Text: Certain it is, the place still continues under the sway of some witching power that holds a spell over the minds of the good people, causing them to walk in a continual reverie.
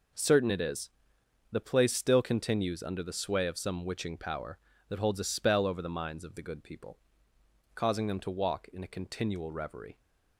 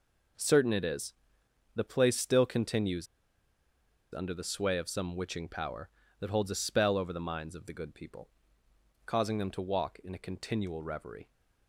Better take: first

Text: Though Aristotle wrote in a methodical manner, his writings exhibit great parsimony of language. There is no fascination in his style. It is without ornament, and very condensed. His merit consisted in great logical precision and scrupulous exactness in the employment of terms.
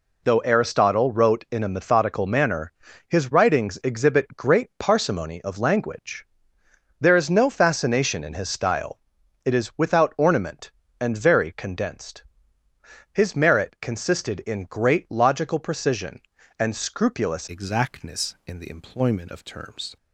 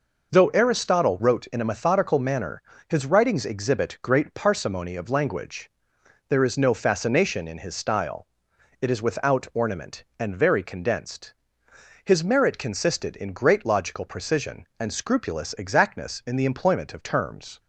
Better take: second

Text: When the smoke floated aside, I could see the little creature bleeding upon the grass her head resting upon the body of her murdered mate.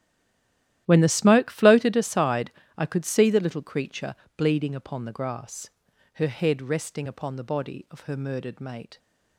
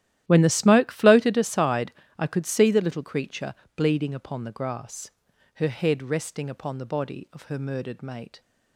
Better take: second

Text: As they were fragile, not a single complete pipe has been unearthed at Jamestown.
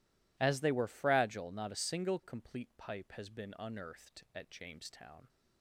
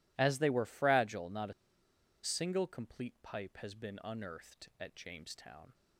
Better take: first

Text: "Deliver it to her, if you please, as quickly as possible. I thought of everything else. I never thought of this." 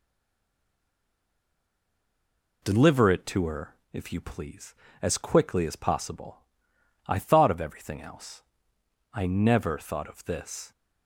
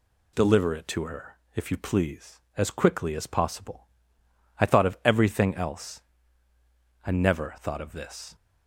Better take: second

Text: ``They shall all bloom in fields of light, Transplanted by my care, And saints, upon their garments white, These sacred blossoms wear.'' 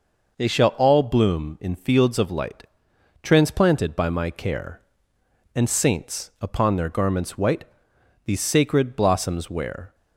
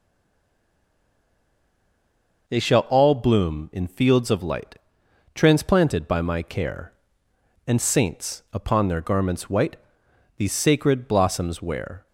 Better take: first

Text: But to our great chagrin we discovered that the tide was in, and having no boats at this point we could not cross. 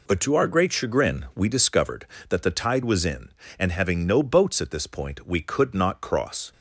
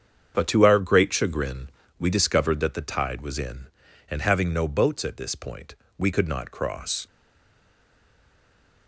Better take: first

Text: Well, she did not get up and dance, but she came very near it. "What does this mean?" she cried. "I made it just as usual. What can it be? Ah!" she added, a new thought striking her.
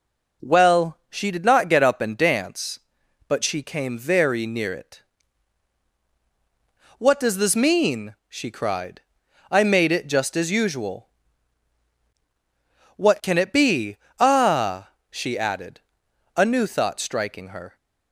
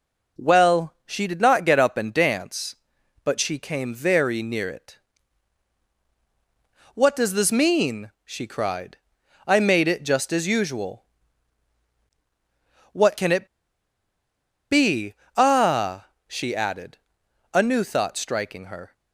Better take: first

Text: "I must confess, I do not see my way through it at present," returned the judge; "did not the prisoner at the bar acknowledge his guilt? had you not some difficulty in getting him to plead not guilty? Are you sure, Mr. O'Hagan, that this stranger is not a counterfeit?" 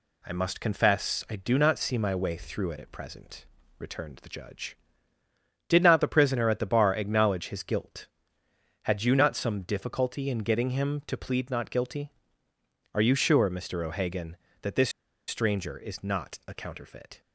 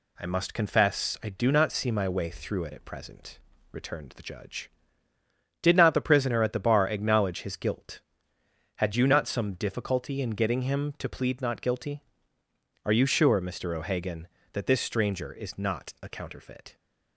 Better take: second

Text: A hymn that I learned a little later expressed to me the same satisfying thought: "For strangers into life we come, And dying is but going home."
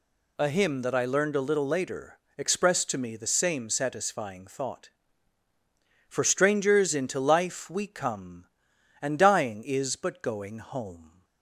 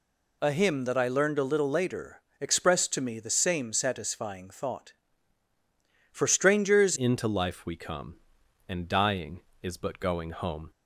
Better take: first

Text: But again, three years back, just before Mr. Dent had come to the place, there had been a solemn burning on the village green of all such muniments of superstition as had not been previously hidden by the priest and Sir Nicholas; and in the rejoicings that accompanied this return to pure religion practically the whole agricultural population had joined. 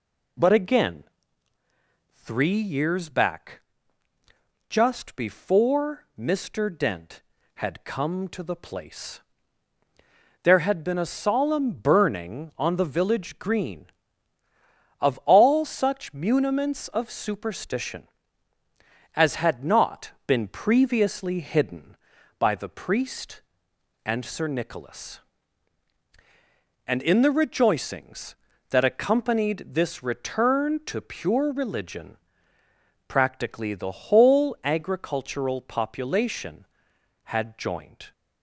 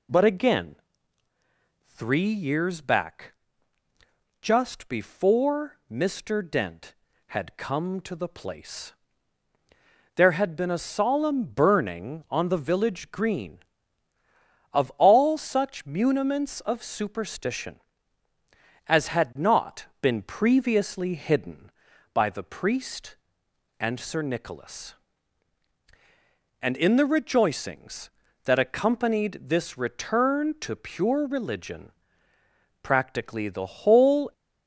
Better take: first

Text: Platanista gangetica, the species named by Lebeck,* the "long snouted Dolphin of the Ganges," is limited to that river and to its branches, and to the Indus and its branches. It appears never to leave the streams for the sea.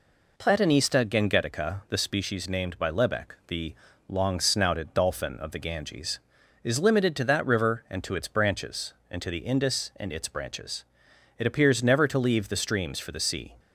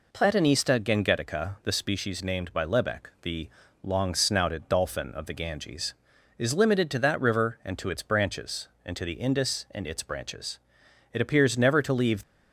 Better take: first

